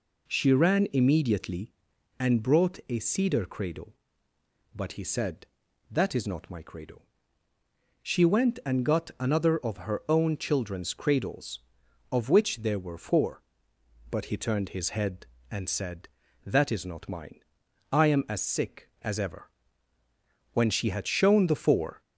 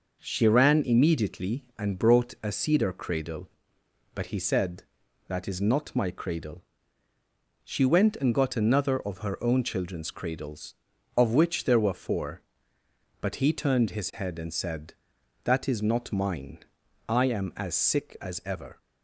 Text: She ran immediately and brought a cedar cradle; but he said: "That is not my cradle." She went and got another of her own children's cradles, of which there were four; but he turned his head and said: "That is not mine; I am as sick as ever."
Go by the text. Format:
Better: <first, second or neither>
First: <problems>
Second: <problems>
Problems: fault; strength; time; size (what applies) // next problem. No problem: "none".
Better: second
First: goes on to say "When she had shown the four"; from 20.5 s on; 1.4 s long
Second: none